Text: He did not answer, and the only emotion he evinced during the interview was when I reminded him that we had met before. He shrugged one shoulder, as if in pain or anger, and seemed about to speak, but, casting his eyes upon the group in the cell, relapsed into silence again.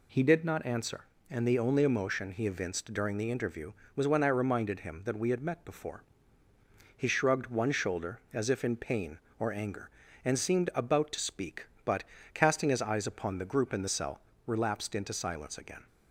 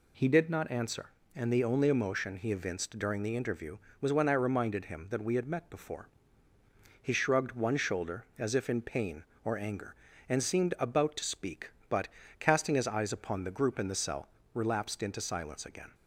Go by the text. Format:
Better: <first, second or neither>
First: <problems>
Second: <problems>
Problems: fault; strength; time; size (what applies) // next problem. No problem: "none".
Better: neither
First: none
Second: none